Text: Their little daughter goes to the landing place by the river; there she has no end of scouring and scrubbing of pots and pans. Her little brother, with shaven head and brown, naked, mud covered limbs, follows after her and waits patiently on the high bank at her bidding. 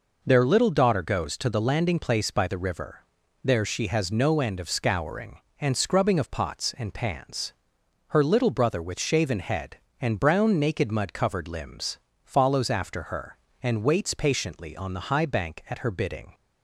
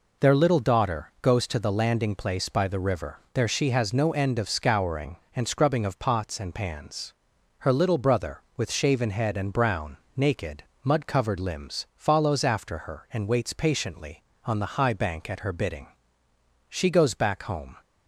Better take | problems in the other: first | goes on to say "She goes back home"; noticeable; from 16.7 s on; 1.0 s long

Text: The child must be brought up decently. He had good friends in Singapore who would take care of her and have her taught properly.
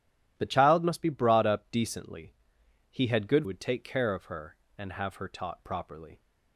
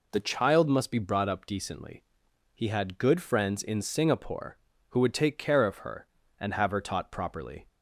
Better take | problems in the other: second | starts louder than the rest; strong; until 1.3 s; 11.5 dB // skips "friends in Singapore who"; at 3.4 s

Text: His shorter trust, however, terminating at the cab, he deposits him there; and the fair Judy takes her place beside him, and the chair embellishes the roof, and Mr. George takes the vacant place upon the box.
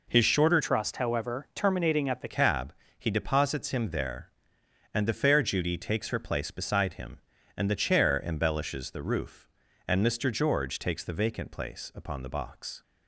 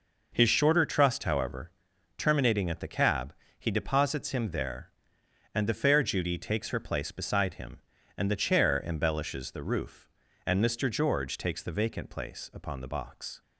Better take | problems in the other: second | changes voice from "trust" to "the"; from 0.6 to 2.2 s; 1.6 s long

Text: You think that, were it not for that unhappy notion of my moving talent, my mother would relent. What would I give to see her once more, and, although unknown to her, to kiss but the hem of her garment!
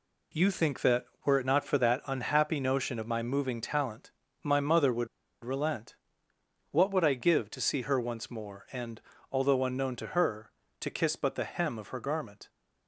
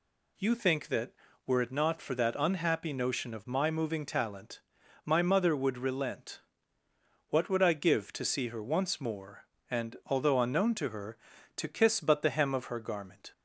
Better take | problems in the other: second | pauses between "would" and "relent"; at 5.0 s; 0.37 s long

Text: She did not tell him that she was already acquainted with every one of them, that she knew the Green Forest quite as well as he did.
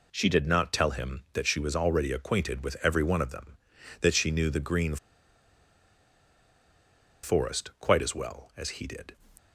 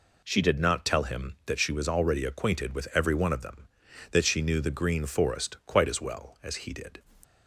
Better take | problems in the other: second | pauses between "Green" and "Forest"; strong; at 4.9 s; 2.2 s long

